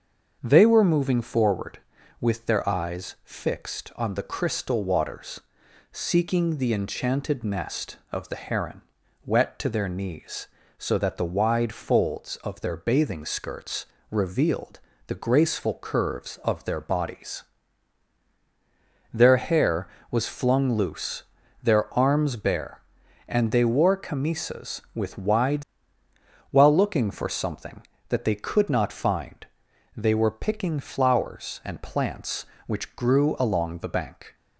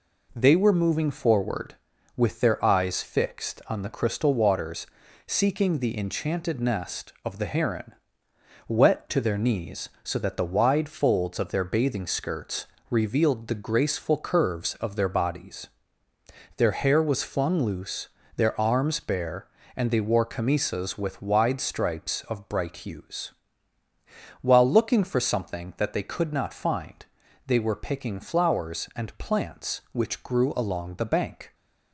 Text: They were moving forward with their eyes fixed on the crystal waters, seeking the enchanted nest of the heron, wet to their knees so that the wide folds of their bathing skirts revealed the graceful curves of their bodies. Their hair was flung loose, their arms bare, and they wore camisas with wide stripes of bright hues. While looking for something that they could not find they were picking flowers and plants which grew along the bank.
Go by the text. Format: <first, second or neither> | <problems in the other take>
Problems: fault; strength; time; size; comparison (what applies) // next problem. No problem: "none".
second | starts louder than the rest; until 1.4 s; 6.5 dB // pauses between "skirts" and "revealed"; slight; at 13.8 s; 0.24 s long; slight in the second // pauses between "revealed" and "the"; slight; at 14.7 s; 0.28 s long // skips "stripes of bright hues"; at 26.0 s // pauses between "find" and "they"; noticeable; at 29.4 s; 0.54 s long; also in the second